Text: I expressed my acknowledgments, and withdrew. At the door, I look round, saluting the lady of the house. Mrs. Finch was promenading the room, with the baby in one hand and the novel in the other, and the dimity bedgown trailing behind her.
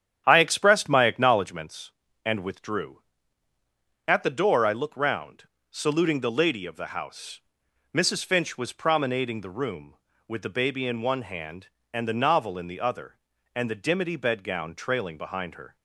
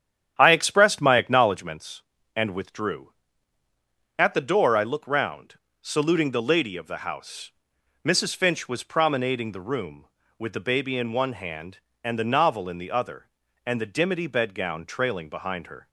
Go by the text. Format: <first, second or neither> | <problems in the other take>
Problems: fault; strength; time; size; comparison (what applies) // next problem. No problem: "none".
neither | starts louder than the rest; strong; the same in both